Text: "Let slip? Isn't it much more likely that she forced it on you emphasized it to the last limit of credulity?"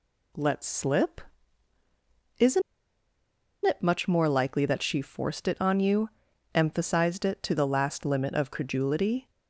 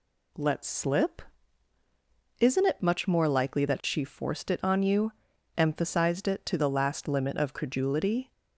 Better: second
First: pauses between "Isn't" and "it"; at 2.6 s; 1.0 s long // pauses between "you" and "emphasized"; at 6.0 s; 0.44 s long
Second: pauses between "you" and "emphasized"; at 5.1 s; 0.44 s long

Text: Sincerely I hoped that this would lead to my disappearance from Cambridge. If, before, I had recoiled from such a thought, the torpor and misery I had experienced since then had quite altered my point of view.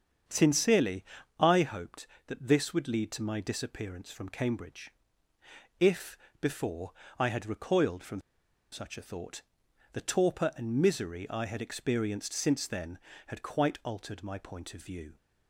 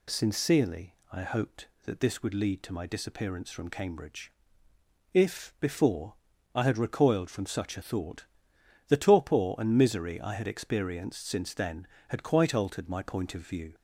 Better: second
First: starts louder than the rest; strong; until 1.6 s; 7.5 dB // pauses between "Sincerely" and "I"; slight; at 1.0 s; 0.34 s long // pauses between "from" and "such"; noticeable; at 8.1 s; 0.51 s long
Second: pauses between "Sincerely" and "I"; slight; at 0.9 s; 0.18 s long

